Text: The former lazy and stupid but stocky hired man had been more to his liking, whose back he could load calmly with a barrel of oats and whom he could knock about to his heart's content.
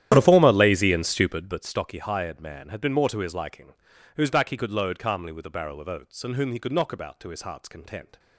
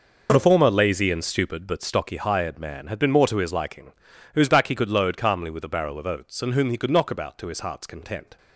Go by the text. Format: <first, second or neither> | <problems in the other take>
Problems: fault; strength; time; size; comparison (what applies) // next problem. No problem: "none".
second | starts louder than the rest; strong; until 1.6 s; 11.5 dB